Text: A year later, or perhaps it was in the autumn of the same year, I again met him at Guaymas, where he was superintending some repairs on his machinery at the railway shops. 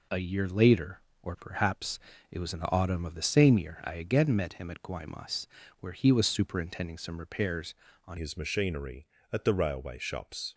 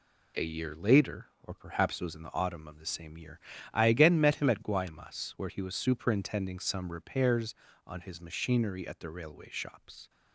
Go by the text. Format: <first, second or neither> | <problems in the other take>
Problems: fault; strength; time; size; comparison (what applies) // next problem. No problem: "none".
second | pauses between "perhaps" and "it"; slight; at 1.9 s; 0.32 s long // changes voice at "his"; from 8.1 s on; 2.4 s long